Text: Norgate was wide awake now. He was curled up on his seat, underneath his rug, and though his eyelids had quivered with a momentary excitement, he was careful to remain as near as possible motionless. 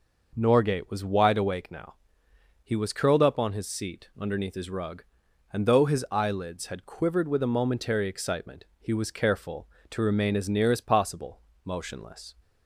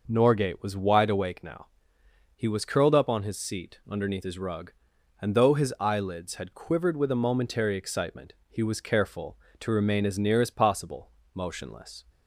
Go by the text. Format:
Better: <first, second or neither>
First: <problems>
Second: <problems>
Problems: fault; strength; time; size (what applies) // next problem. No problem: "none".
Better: neither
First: pauses between "possible" and "motionless"; slight; at 11.4 s; 0.24 s long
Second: pauses between "possible" and "motionless"; slight; at 11.1 s; 0.24 s long